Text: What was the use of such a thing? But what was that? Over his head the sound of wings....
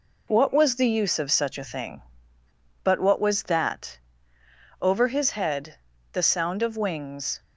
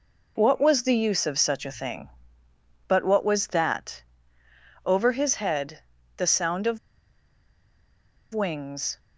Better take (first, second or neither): first